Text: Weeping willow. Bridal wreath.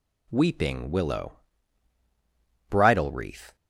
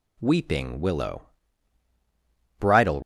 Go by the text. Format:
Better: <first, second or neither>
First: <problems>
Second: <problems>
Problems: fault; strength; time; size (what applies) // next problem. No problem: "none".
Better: first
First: none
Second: stops before "wreath"; at 3.0 s